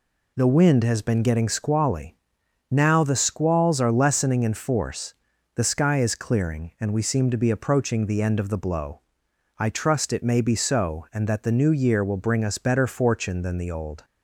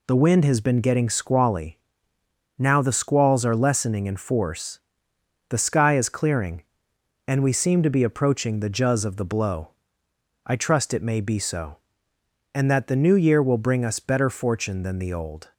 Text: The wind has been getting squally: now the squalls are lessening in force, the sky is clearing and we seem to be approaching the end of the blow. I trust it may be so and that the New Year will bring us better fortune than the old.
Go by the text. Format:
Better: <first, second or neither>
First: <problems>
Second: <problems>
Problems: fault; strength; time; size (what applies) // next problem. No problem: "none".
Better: first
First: none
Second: says "juz" for "end"; at 8.6 s